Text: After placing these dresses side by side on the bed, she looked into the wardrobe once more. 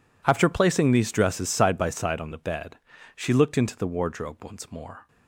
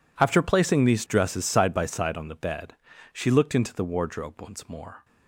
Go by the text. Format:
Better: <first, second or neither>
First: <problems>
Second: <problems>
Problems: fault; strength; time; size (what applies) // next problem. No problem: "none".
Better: neither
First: none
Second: none